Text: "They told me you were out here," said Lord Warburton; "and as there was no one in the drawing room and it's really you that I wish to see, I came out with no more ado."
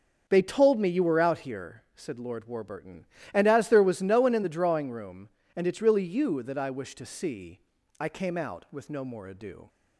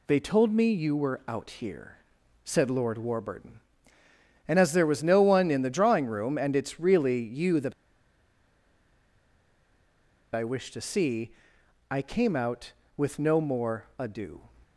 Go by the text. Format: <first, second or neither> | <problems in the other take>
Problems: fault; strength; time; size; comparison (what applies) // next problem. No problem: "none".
first | pauses between "that" and "I"; strong; at 7.7 s; 2.5 s long